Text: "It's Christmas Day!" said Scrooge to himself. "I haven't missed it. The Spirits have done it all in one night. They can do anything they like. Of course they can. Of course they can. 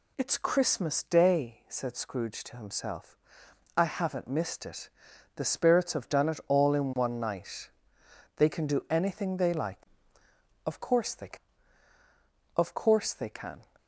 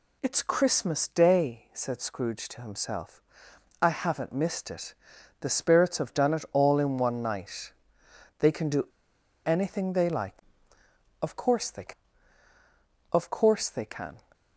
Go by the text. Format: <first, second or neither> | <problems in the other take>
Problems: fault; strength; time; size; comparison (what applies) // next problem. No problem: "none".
first | pauses between "do" and "anything"; noticeable; at 8.8 s; 0.59 s long